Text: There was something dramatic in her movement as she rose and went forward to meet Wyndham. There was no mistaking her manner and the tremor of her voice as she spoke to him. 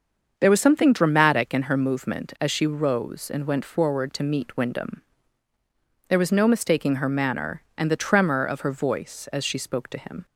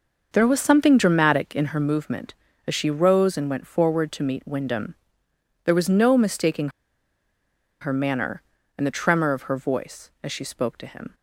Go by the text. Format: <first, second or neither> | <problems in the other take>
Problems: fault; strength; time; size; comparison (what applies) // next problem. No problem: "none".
first | starts louder than the rest; until 1.3 s; 6 dB; also in the first // pauses between "mistaking" and "her"; at 6.7 s; 1.1 s long